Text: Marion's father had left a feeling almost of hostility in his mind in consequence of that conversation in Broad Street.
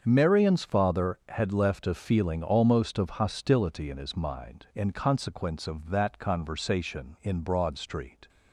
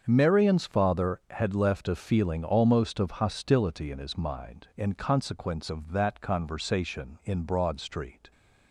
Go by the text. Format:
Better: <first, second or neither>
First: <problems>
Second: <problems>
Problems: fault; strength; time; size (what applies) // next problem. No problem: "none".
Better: neither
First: starts louder than the rest; until 1.0 s; 7 dB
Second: starts louder than the rest; until 1.0 s; 7 dB